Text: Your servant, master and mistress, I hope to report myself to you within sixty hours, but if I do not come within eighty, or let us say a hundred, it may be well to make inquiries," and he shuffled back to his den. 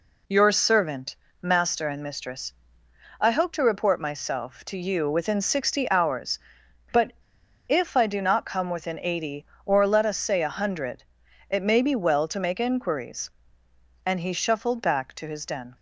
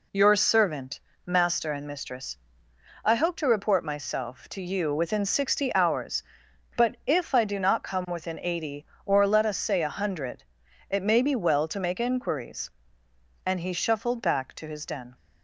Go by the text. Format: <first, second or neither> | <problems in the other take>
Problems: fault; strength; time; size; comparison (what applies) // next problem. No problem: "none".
second | pauses between "but" and "if"; noticeable; at 7.1 s; 0.55 s long